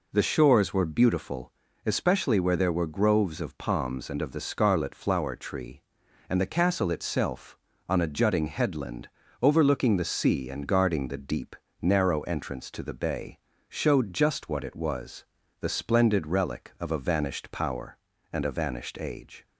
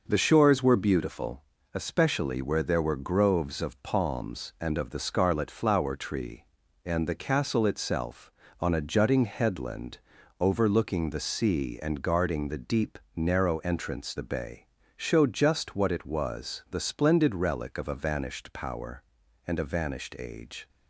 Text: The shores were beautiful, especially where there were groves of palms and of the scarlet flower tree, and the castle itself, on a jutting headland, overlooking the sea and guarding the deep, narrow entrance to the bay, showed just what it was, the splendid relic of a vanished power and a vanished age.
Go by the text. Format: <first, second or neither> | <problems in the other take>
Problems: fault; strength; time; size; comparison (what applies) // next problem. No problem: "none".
first | skips "to"; at 14.1 s